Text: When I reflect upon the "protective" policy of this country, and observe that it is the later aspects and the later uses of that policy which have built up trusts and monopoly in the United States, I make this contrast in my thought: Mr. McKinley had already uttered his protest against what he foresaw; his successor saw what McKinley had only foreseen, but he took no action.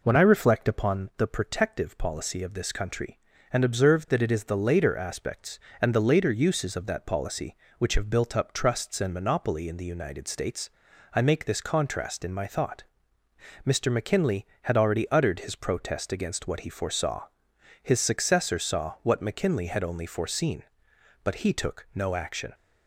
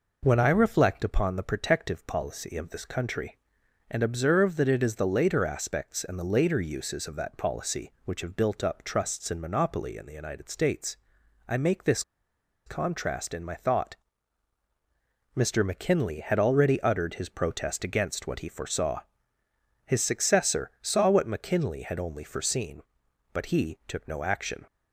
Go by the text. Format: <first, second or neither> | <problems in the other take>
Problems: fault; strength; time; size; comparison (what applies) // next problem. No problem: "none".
first | pauses between "this" and "contrast"; noticeable; at 12.0 s; 0.62 s long